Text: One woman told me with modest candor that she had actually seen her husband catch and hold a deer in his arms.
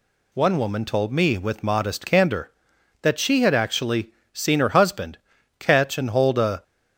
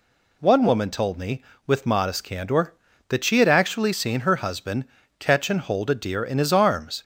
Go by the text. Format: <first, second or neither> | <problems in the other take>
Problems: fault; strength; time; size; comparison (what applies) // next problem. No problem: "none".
second | pauses between "actually" and "seen"; slight; at 4.1 s; 0.20 s long // pauses between "husband" and "catch"; at 5.1 s; 0.44 s long; slight in the second // stops before "deer in his arms"; at 6.6 s